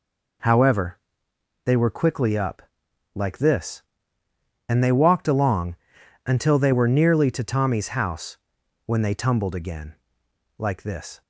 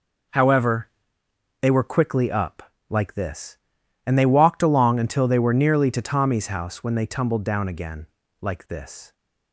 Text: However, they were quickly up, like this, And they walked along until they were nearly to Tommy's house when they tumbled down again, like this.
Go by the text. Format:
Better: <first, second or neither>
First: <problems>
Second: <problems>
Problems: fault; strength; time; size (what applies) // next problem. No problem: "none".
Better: second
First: pauses between "along" and "until"; noticeable; at 5.7 s; 0.50 s long // pauses between "house" and "when"; noticeable; at 8.3 s; 0.48 s long // skips "down"; at 9.5 s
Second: none